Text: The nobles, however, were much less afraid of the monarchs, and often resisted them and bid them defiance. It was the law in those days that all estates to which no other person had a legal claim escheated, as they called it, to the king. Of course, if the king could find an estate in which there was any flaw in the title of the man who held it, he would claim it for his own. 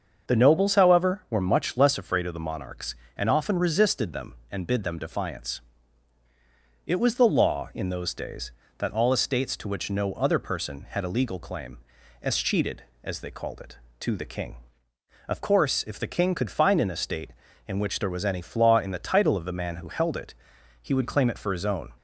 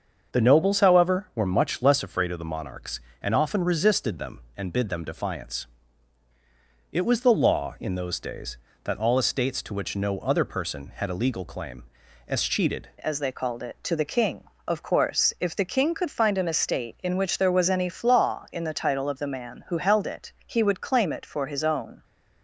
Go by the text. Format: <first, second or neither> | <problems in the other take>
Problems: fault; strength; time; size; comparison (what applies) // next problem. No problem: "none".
first | starts louder than the rest; until 1.4 s; 6.5 dB; also in the first // pauses between "claim" and "escheated"; noticeable; at 11.8 s; 0.46 s long; noticeable in the first // changes voice at "as"; from 12.9 s on; 9.1 s long